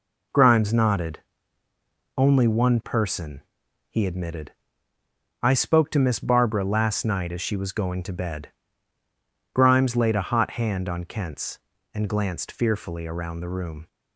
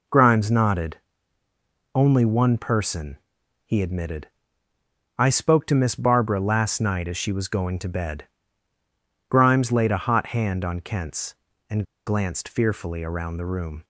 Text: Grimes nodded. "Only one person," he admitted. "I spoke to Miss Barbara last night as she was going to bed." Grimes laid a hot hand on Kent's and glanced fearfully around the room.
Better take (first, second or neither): first